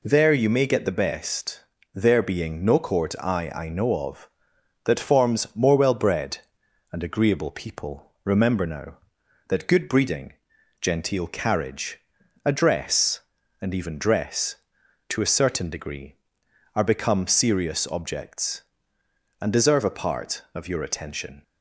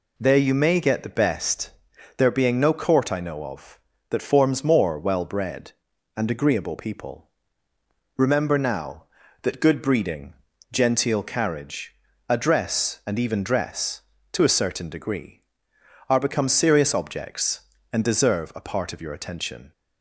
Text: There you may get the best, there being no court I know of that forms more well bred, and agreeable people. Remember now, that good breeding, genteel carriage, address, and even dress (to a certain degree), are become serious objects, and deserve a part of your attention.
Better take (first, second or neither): second